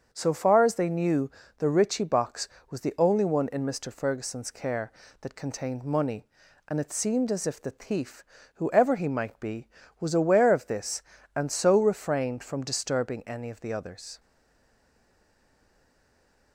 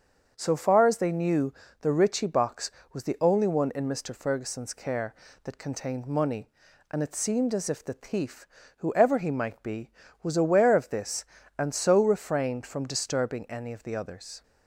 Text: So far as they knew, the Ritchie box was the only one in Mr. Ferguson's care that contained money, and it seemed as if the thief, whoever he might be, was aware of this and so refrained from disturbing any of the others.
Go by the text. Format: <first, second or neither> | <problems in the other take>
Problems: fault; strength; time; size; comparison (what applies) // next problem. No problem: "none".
second | starts louder than the rest; until 1.1 s; 7 dB; also in the second // stays silent after the last word; from 14.1 s on; 2.4 s long